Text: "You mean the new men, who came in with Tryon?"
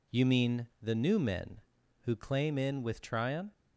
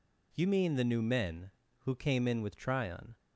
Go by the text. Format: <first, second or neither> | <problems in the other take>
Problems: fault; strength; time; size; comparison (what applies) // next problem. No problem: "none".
second | says "claim" for "came"; at 2.1 s